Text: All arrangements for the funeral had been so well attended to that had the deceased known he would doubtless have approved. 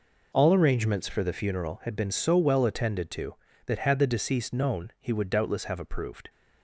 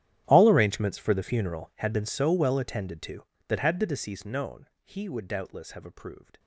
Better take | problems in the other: first | gets quieter; strong; throughout; 21.5 dB // pauses between "known" and "he"; slight; at 4.6 s; 0.16 s long

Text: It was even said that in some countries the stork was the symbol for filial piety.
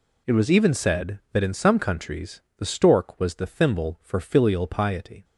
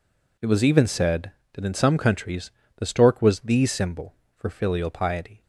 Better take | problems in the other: second | pauses between "countries" and "the"; slight; at 2.4 s; 0.16 s long; slight in the second // says "thimble" for "symbol"; at 3.4 s

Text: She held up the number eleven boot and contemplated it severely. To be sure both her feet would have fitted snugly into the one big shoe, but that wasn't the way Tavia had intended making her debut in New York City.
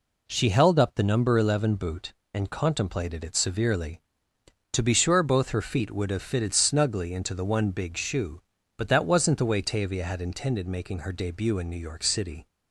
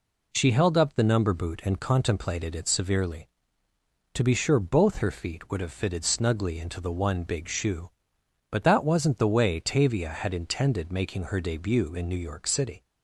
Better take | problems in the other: first | skips "eleven"; at 1.3 s

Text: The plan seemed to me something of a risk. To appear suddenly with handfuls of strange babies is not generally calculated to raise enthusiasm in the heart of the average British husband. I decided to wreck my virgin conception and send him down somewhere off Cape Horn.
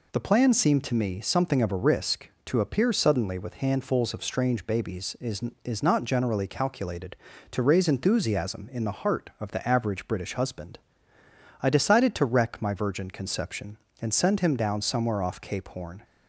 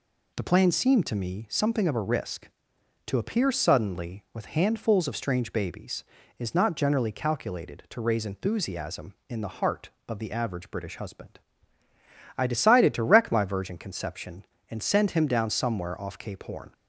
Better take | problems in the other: second | says "is" twice; at 5.6 s

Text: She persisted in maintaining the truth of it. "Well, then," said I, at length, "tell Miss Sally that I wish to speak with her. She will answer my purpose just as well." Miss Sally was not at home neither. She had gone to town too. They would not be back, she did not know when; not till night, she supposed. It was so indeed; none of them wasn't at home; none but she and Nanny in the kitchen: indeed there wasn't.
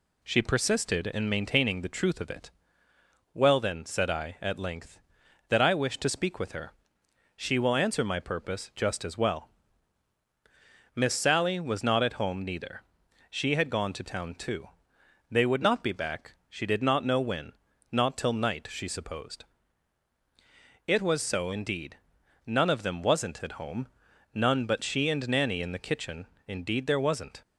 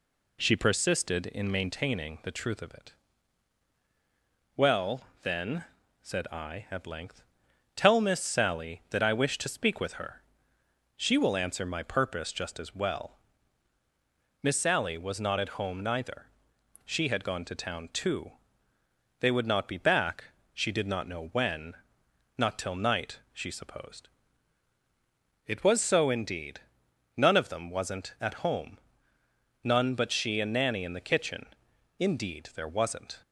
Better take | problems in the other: second | skips "tell Miss Sally"; at 5.2 s

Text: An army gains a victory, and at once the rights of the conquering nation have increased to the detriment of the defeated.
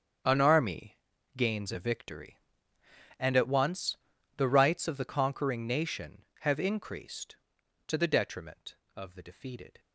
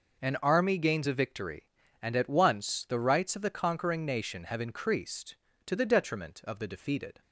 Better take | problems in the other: second | gets quieter; strong; throughout; 13.5 dB // pauses between "army" and "gains"; slight; at 0.9 s; 0.36 s long // pauses between "once" and "the"; at 3.9 s; 0.40 s long

